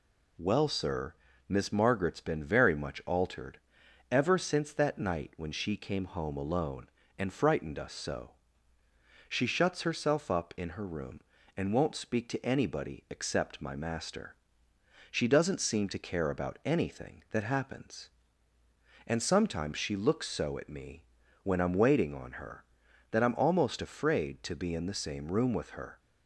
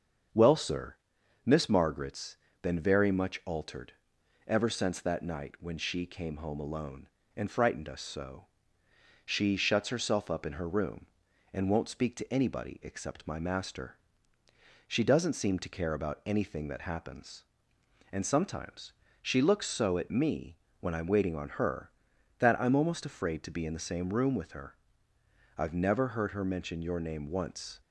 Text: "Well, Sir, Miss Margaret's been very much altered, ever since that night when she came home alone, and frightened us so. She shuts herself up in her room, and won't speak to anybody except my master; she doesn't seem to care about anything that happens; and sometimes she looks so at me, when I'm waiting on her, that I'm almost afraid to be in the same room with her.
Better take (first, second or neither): first